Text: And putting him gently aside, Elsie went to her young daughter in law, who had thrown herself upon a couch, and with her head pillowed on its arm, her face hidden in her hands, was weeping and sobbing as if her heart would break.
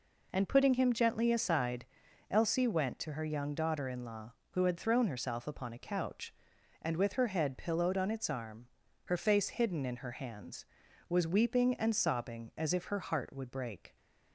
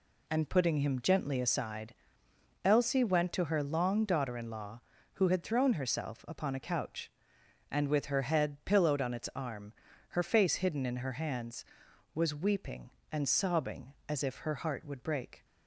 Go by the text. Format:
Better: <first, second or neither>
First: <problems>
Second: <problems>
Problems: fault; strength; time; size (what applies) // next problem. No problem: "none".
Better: first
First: none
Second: says "long" for "young"; at 3.6 s